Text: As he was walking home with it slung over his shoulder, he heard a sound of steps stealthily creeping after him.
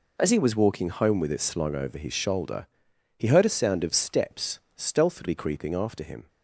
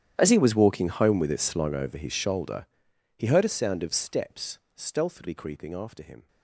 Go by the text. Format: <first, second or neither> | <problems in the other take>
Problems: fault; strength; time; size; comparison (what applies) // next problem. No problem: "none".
first | gets quieter; strong; throughout; 21.5 dB // pauses between "steps" and "stealthily"; slight; at 4.5 s; 0.18 s long; slight in the first